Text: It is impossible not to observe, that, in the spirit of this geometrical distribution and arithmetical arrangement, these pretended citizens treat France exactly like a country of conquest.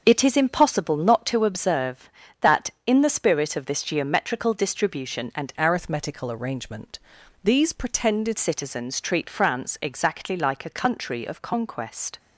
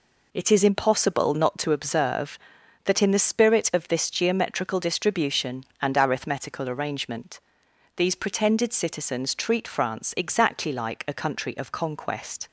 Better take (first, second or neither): second